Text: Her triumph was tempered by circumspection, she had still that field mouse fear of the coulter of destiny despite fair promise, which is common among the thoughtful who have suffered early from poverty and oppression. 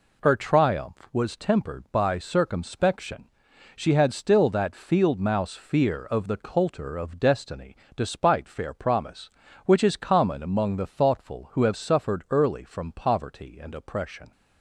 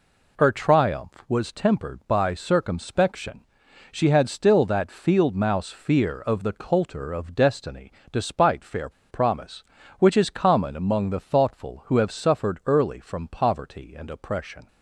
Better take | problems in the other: first | pauses between "destiny" and "despite"; slight; at 7.9 s; 0.18 s long; slight in the first // pauses between "fair" and "promise"; slight; at 8.8 s; 0.20 s long

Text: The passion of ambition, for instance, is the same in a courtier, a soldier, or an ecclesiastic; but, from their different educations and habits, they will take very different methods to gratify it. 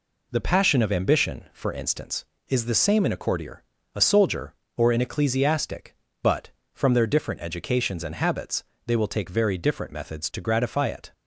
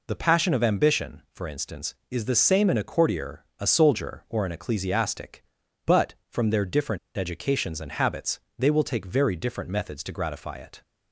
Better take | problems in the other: first | pauses between "different" and "educations"; slight; at 6.9 s; 0.19 s long

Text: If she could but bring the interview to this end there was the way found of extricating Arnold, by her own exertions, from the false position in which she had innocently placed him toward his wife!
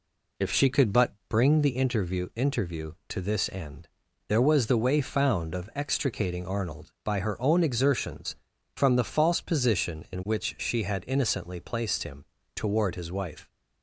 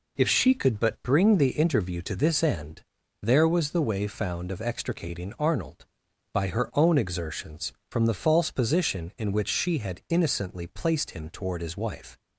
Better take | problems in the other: second | pauses between "but" and "bring"; slight; at 1.1 s; 0.16 s long // says "interview" twice; at 2.3 s // pauses between "end" and "there"; at 3.8 s; 0.40 s long; also in the second // pauses between "him" and "toward"; slight; at 12.2 s; 0.30 s long

